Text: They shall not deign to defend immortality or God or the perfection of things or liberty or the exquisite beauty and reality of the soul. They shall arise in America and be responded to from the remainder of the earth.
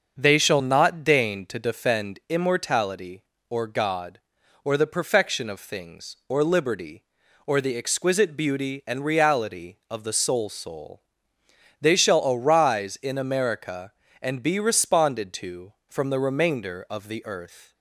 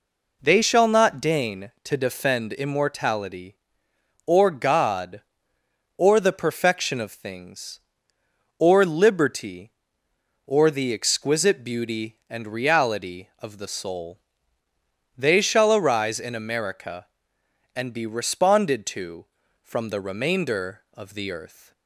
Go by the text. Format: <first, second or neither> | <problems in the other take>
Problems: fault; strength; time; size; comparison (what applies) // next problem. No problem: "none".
second | starts louder than the rest; until 1.2 s; 6.5 dB // says "soul" twice; at 10.4 s